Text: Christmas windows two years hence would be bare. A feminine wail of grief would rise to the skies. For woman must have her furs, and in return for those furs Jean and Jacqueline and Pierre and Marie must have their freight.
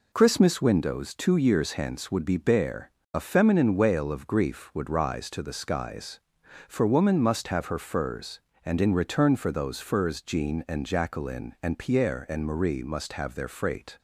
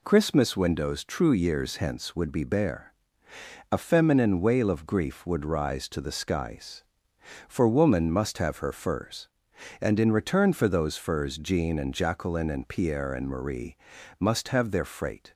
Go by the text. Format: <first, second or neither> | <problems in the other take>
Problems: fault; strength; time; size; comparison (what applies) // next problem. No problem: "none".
first | says "true" for "two"; at 1.0 s // pauses between "Marie" and "must"; at 13.7 s; 0.42 s long